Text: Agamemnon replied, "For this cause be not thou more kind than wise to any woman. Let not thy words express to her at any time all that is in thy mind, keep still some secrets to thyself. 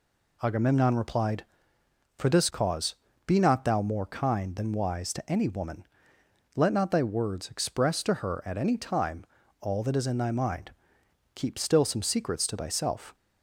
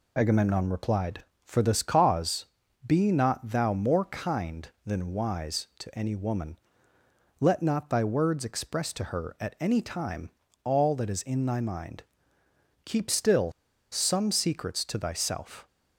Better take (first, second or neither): first